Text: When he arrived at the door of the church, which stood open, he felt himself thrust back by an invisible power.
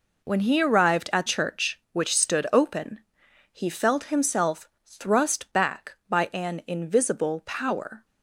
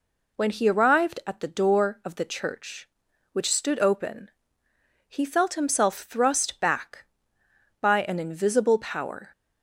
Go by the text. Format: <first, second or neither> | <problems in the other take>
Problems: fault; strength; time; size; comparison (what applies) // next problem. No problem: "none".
second | skips "the door of the"; at 1.2 s // pauses between "himself" and "thrust"; slight; at 4.6 s; 0.16 s long